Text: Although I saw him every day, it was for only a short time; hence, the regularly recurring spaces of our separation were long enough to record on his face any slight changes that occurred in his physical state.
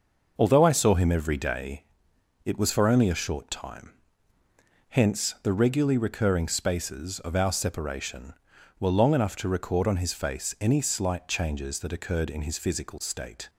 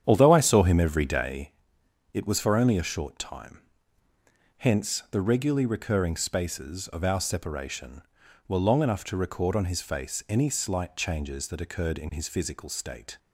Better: first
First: none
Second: starts louder than the rest; strong; until 1.5 s; 9 dB

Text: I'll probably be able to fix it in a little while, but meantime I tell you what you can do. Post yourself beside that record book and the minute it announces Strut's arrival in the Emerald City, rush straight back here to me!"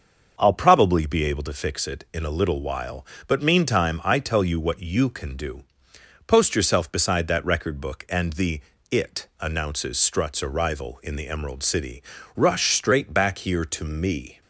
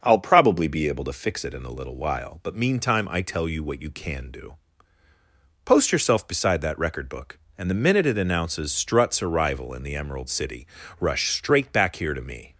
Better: second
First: starts louder than the rest; until 1.3 s; 6 dB // skips "minute"; at 8.7 s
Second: starts louder than the rest; until 1.0 s; 6.5 dB

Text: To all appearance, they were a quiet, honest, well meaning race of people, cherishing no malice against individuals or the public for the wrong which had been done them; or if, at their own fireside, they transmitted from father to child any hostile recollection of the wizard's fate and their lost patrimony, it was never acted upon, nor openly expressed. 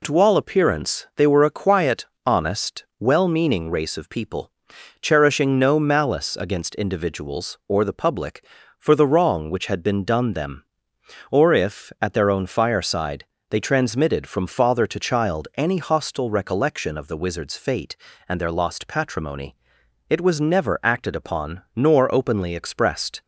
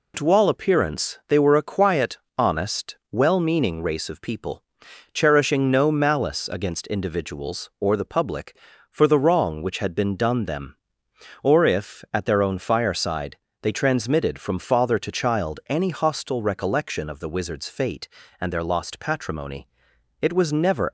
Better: first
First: none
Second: stops before "acted upon nor openly expressed"; at 20.8 s

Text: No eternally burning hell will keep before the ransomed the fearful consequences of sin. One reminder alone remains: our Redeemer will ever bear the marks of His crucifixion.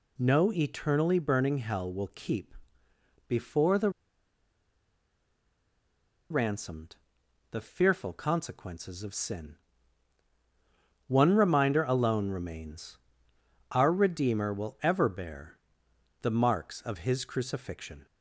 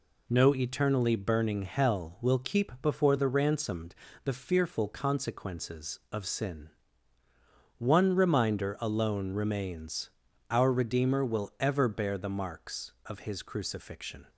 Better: second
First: pauses between "keep" and "before"; noticeable; at 2.5 s; 0.74 s long // pauses between "the" and "ransomed"; strong; at 3.8 s; 2.4 s long // pauses between "ransomed" and "the"; noticeable; at 6.9 s; 0.54 s long // pauses between "bear" and "the"; noticeable; at 15.5 s; 0.64 s long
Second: pauses between "ransomed" and "the"; slight; at 3.9 s; 0.30 s long

